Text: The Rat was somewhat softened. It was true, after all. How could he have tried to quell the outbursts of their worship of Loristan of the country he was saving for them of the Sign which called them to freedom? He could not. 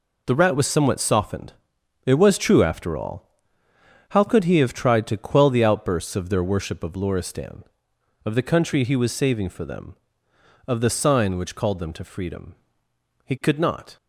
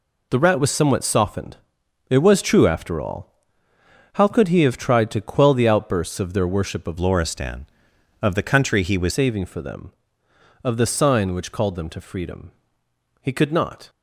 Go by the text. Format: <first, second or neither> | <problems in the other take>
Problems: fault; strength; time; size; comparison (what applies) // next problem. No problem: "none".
first | changes voice from "Loristan" to "was"; from 6.9 to 9.1 s; 2.2 s long